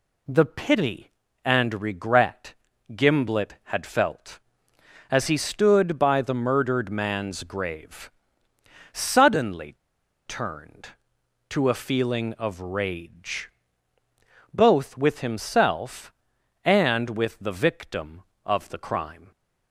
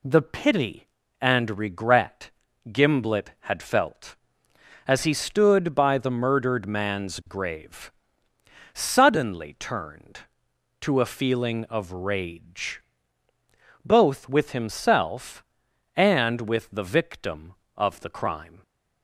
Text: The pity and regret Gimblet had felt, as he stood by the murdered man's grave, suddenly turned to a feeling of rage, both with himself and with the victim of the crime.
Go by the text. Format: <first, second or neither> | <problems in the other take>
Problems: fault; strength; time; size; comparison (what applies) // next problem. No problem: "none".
second | pauses between "regret" and "Gimblet"; at 2.5 s; 0.40 s long; also in the second // pauses between "suddenly" and "turned"; noticeable; at 9.7 s; 0.53 s long